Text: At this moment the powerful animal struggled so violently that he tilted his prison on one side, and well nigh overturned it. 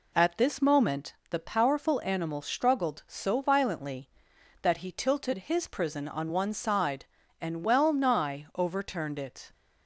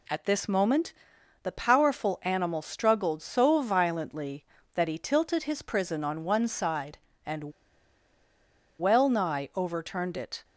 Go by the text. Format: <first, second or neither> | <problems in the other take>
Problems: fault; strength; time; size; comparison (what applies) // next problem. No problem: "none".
first | pauses between "moment" and "the"; noticeable; at 0.9 s; 0.50 s long // pauses between "and" and "well"; strong; at 7.5 s; 1.2 s long